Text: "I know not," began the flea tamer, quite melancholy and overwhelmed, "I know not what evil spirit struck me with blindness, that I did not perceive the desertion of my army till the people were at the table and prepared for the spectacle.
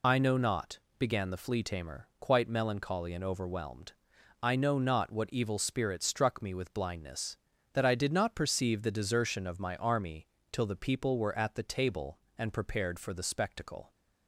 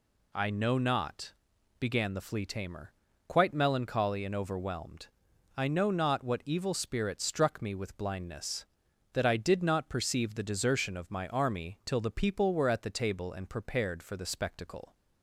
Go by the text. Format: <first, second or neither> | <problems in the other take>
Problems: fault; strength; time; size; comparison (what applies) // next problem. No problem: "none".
second | loses the start of "I"; at 0.0 s; 50 ms // pauses between "army" and "till"; slight; at 10.2 s; 0.26 s long